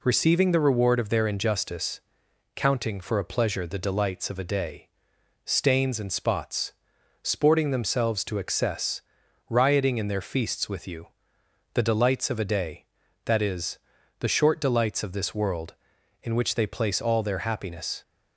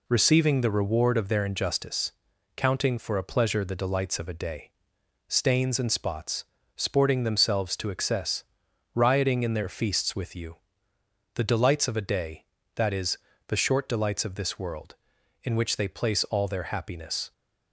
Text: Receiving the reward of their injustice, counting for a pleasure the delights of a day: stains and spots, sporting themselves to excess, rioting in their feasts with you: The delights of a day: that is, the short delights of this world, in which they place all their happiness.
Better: neither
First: none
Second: none

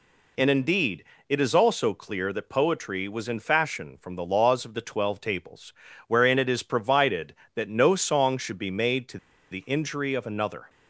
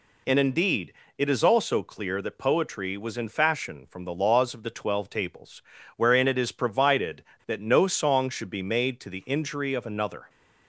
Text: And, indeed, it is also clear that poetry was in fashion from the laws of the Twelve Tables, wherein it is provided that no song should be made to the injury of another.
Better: second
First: pauses between "to" and "the"; slight; at 9.1 s; 0.34 s long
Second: none

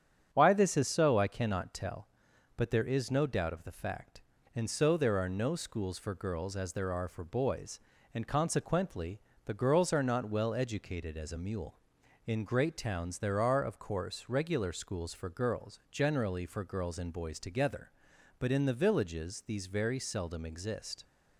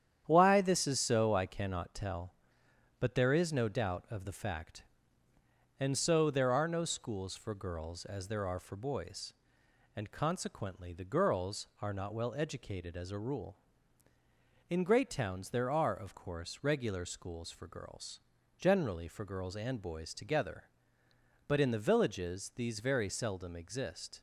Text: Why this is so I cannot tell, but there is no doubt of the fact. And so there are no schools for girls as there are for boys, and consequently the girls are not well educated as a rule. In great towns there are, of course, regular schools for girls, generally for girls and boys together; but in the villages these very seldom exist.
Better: second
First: starts louder than the rest; strong; until 1.3 s; 8 dB // pauses between "consequently" and "the"; slight; at 9.1 s; 0.24 s long // says "mule" for "rule"; at 11.3 s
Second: starts louder than the rest; strong; until 1.2 s; 9.5 dB

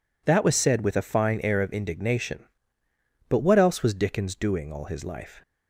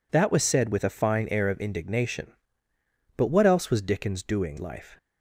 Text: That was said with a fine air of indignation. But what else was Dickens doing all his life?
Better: first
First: none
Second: skips "all his"; at 4.5 s

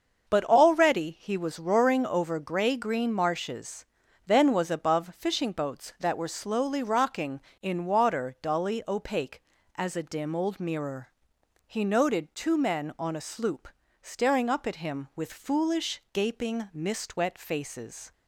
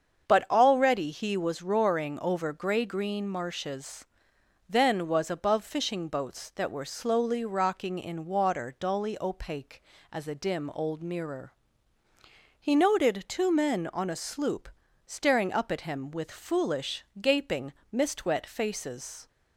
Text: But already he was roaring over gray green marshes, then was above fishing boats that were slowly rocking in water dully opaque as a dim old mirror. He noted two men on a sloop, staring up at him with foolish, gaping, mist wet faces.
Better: neither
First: starts louder than the rest; until 1.3 s; 6.5 dB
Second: starts louder than the rest; strong; until 1.3 s; 7 dB

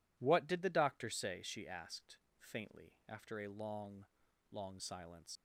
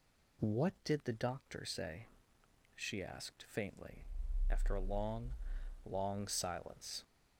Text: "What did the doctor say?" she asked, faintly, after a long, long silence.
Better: second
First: leaves "silence" unfinished; at 5.3 s; 90 ms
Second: none

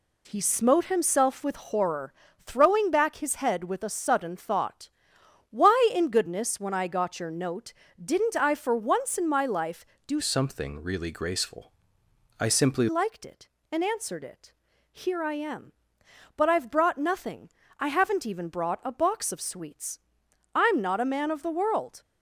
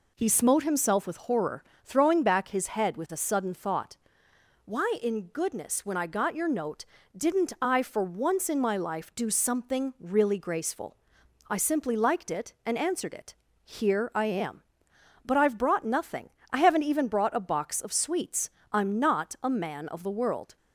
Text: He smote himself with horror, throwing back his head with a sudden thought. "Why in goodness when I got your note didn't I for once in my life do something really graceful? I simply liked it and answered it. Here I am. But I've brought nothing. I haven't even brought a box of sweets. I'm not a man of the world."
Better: second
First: pauses between "note" and "didn't"; slight; at 7.7 s; 0.32 s long // changes voice from "something" to "simply"; from 10.1 to 12.8 s; 2.7 s long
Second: pauses between "note" and "didn't"; slight; at 6.8 s; 0.28 s long

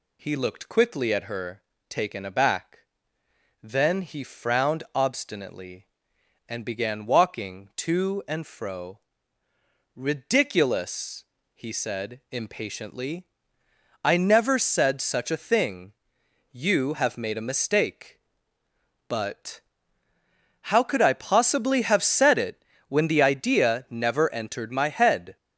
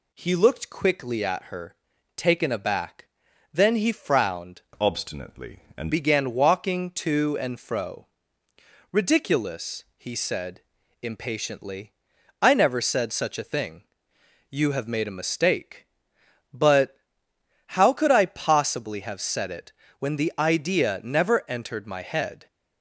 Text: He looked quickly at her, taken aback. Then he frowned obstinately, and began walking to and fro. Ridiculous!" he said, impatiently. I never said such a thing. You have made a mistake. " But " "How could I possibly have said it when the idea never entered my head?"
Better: first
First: pauses between "it" and "when"; slight; at 22.6 s; 0.24 s long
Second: changes voice from "obstinately" to "and"; from 4.7 to 5.9 s; 1.2 s long // pauses between "it" and "when"; slight; at 19.7 s; 0.26 s long

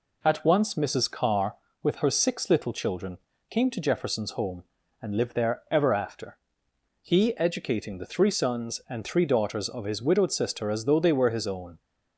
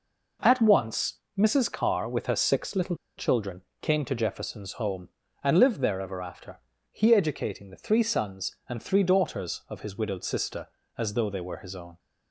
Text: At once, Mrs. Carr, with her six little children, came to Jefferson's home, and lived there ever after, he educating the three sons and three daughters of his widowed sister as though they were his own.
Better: first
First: none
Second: pauses between "little" and "children"; slight; at 2.9 s; 0.22 s long

